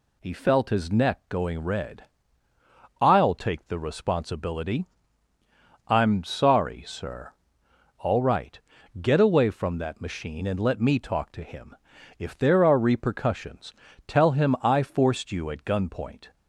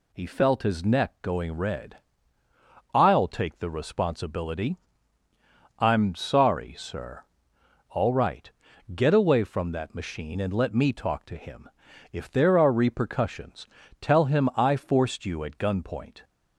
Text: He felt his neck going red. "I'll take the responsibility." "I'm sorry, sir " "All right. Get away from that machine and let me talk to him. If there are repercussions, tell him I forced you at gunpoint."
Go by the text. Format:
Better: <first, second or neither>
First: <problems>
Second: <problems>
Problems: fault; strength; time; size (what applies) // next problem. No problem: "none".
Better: neither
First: none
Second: none